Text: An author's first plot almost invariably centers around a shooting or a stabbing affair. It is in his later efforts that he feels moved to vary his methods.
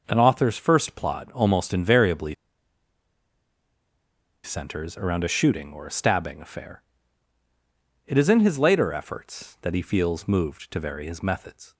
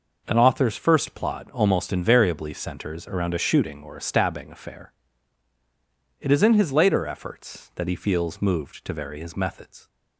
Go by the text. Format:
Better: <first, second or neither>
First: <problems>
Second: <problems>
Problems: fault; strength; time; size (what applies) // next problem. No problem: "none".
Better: second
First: pauses between "invariably" and "centers"; strong; at 2.3 s; 2.0 s long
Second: none